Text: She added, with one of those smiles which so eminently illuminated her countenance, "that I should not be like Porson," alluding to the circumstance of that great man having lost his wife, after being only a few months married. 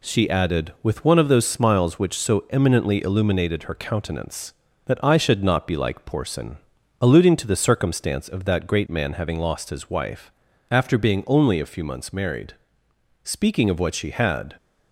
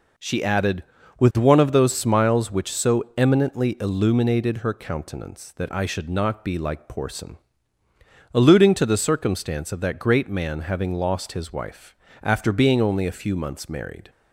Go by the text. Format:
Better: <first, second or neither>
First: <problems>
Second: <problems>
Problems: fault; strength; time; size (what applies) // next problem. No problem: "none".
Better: second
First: goes on to say "Speaking of what she had"; from 13.2 s on; 1.3 s long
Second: none